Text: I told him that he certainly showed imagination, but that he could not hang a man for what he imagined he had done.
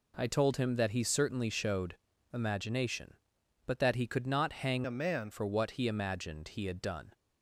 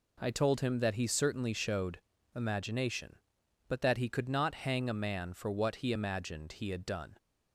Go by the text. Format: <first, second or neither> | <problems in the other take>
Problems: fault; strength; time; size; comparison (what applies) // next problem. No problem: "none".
second | pauses between "showed" and "imagination"; slight; at 1.9 s; 0.36 s long; slight in the second // changes voice from "a" to "man"; from 4.8 to 5.3 s; 0.5 s long